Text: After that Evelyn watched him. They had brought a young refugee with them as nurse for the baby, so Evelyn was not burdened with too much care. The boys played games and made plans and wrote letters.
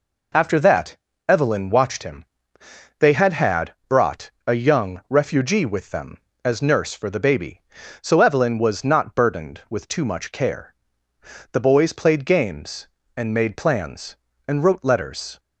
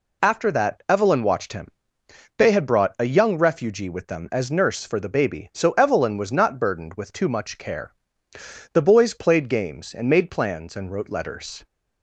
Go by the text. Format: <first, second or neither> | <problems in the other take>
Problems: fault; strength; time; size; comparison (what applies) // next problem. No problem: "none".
second | pauses between "that" and "Evelyn"; slight; at 0.9 s; 0.32 s long // says "had" twice; at 3.3 s // pauses between "brought" and "a"; slight; at 4.3 s; 0.16 s long